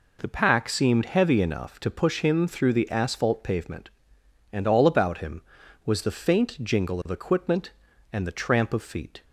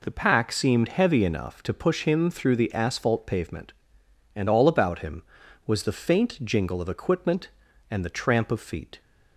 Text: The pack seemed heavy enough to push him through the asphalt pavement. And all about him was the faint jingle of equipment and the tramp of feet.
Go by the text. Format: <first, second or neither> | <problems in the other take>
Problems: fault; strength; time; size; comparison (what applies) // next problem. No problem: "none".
neither | none